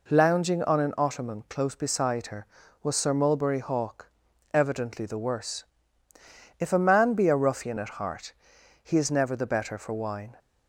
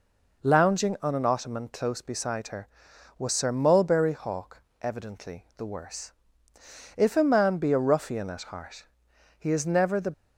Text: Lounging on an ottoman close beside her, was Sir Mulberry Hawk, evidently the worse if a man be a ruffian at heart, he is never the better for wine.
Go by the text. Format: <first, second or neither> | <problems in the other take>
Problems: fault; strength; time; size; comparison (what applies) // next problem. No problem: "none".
first | pauses between "worse" and "if"; noticeable; at 6.1 s; 0.86 s long; noticeable in the first // stops before "better for wine"; at 10.1 s